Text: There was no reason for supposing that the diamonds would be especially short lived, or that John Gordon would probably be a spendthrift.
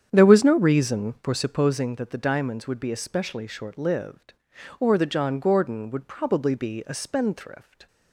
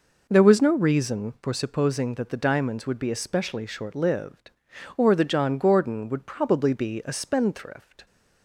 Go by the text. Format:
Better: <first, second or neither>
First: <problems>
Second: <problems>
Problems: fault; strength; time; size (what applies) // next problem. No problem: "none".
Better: second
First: starts louder than the rest; strong; until 2.0 s; 8.5 dB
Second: none